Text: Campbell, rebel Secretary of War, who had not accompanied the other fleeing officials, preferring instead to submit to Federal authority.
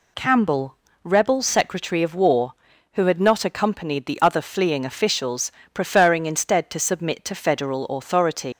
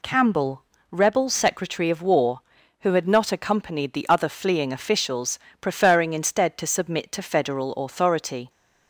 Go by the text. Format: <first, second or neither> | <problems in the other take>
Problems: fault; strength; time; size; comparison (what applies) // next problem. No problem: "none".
second | leaves "authority" unfinished; at 8.5 s; 95 ms